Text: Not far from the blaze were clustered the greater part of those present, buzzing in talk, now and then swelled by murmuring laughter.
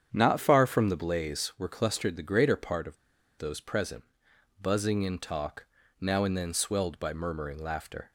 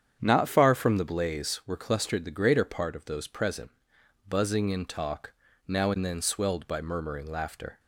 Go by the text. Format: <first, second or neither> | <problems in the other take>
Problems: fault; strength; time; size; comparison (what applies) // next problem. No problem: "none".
second | starts louder than the rest; strong; until 1.1 s; 8.5 dB; strong in the second // pauses between "of" and "those"; at 2.9 s; 0.41 s long